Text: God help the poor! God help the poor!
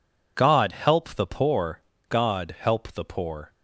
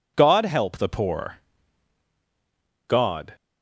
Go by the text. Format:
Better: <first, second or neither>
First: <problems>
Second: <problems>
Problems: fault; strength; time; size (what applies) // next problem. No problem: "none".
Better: first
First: none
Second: stops before "help the poor"; at 3.3 s